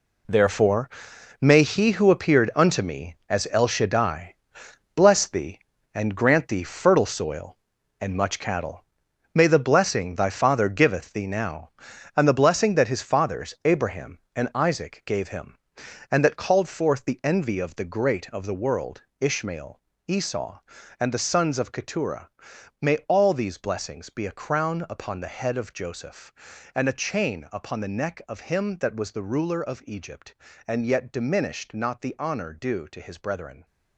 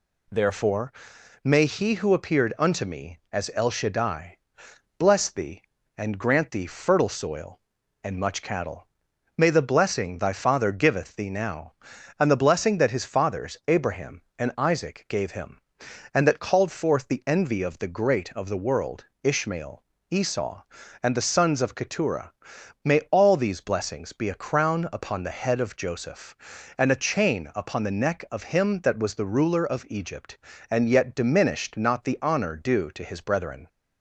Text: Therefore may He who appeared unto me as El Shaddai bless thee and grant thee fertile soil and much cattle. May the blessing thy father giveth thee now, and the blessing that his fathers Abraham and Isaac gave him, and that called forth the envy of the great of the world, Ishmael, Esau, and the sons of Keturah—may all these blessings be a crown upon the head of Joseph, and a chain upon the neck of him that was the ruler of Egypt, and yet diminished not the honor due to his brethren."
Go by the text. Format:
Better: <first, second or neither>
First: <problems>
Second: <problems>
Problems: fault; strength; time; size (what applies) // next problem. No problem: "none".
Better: second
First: gets quieter; strong; throughout; 11.5 dB // pauses between "Therefore" and "may"; noticeable; at 0.8 s; 0.50 s long // pauses between "Shaddai" and "bless"; noticeable; at 4.3 s; 0.62 s long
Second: pauses between "Therefore" and "may"; noticeable; at 0.9 s; 0.50 s long // pauses between "Shaddai" and "bless"; noticeable; at 4.3 s; 0.62 s long